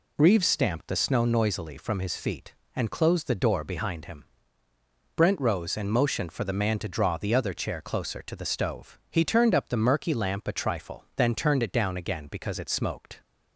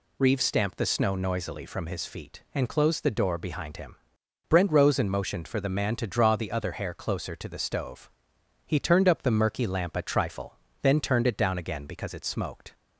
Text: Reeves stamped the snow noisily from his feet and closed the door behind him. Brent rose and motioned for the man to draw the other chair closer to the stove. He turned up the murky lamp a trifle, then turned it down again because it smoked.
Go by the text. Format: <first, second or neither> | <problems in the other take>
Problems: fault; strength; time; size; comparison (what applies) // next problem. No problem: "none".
first | says "hair" for "chair"; at 6.7 s